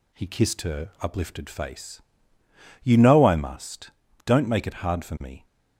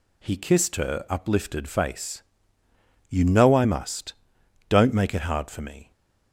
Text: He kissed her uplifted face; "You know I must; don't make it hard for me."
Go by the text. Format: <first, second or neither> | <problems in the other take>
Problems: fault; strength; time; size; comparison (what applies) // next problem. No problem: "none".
neither | none